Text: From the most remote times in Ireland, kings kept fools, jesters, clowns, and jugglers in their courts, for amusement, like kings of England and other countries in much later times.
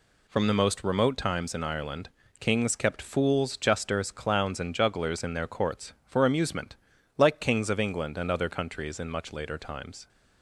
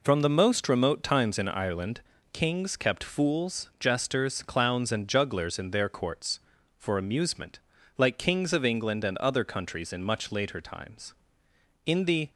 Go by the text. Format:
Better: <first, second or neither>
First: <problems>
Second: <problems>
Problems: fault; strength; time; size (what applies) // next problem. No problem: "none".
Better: first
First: none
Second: goes on to say "In the"; slight; from 11.8 s on; 0.46 s long